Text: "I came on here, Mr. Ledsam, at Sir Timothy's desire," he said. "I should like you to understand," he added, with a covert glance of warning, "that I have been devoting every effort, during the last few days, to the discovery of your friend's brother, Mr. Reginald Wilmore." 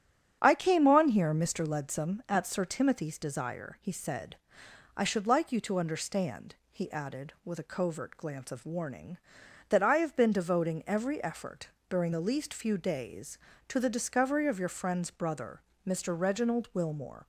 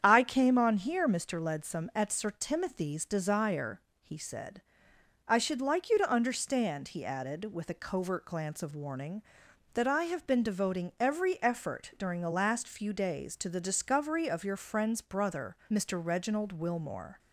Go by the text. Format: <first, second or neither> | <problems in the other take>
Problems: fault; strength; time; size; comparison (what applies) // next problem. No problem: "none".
second | starts louder than the rest; strong; until 1.4 s; 9.5 dB; strong in the second // says "least" for "last"; at 12.1 s